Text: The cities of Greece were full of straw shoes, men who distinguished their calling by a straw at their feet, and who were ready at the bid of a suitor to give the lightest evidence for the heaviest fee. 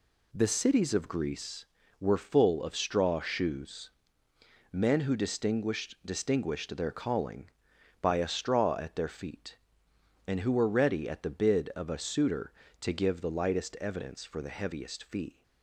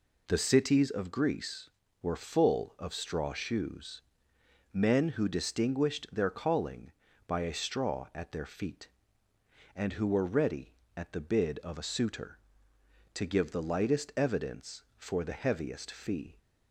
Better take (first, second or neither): second